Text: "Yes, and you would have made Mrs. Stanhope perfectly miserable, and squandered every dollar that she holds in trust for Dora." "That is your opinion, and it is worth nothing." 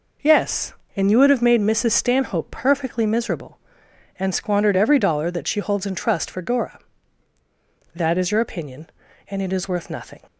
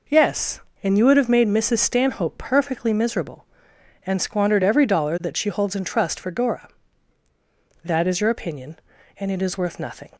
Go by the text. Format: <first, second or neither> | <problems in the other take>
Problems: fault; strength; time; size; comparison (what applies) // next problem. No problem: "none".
neither | none